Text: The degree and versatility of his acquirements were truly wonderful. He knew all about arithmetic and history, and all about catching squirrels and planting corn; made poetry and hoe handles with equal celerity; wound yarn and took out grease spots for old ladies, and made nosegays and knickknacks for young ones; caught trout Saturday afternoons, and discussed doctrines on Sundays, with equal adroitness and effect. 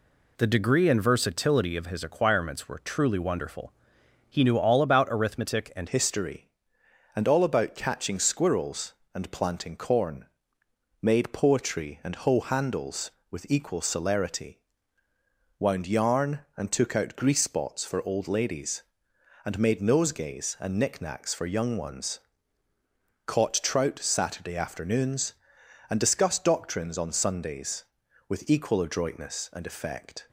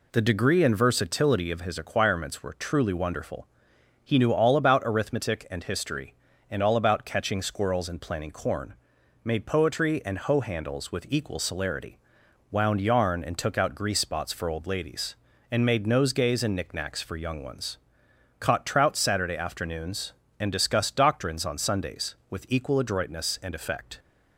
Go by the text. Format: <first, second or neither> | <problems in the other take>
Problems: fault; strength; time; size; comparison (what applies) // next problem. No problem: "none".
second | changes voice at "history"; from 5.8 s on; 24.4 s long